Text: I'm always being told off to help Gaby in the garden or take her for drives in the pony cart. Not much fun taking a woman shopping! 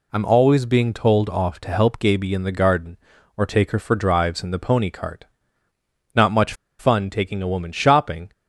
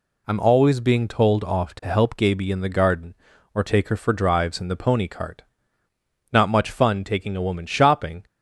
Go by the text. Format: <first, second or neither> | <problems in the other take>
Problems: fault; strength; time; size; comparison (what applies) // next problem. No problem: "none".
second | pauses between "much" and "fun"; slight; at 6.5 s; 0.25 s long